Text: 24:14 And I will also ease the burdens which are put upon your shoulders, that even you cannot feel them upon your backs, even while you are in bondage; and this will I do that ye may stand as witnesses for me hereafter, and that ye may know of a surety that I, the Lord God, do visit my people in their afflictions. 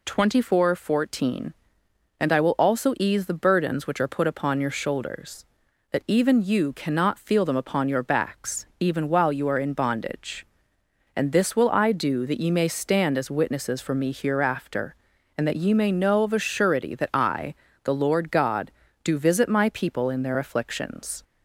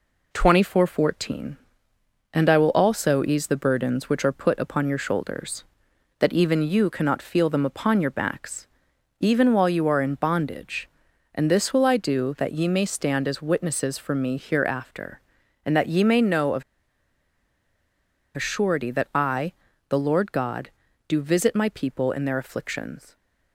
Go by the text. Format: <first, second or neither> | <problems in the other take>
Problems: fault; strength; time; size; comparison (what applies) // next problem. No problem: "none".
first | pauses between "of" and "a"; strong; at 16.6 s; 1.7 s long